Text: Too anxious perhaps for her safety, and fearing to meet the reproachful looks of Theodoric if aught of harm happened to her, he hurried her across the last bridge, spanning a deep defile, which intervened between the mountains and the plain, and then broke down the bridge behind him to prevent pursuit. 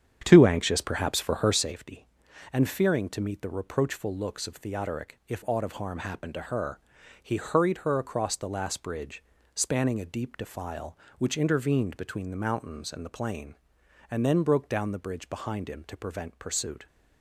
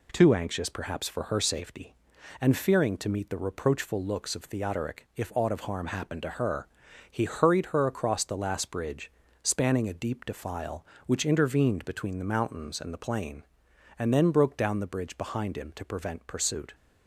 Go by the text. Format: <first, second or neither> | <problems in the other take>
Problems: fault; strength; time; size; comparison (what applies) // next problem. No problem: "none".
second | starts louder than the rest; strong; until 1.6 s; 8.5 dB